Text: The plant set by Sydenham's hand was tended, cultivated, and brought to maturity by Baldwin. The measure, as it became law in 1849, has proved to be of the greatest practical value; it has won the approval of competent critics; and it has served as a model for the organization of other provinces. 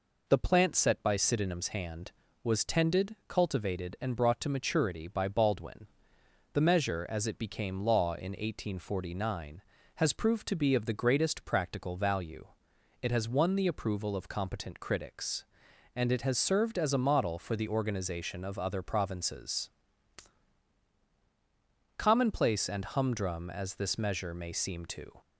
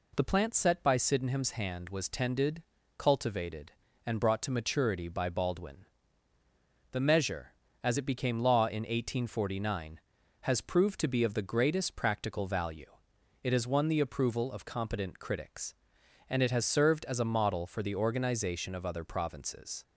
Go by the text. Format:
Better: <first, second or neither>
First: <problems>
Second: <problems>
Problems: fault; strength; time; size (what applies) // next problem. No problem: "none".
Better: second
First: goes on to say "Commonplace and humdrum as this measure may seem to"; strong; from 21.9 s on; 3.2 s long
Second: none